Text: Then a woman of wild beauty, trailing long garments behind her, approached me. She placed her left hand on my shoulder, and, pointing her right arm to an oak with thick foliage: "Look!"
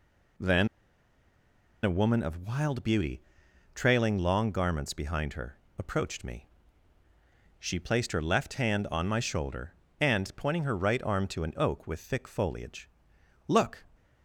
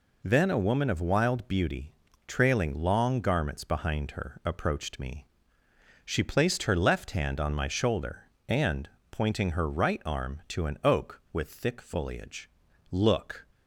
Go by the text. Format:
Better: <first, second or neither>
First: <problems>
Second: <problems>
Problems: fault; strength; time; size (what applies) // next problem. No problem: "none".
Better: second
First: pauses between "Then" and "a"; at 0.6 s; 1.1 s long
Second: none